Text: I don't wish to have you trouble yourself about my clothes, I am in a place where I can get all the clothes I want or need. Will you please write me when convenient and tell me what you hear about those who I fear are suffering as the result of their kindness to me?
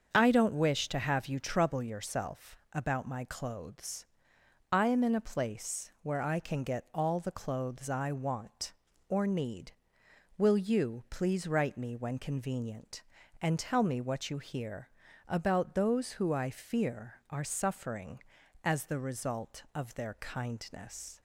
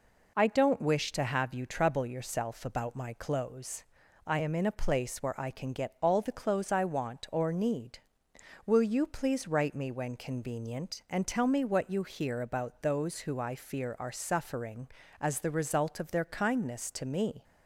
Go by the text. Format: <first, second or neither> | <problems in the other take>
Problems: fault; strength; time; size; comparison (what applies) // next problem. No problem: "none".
second | starts louder than the rest; until 1.1 s; 7 dB // pauses between "hear" and "about"; at 14.8 s; 0.40 s long // stops before "to me"; at 21.1 s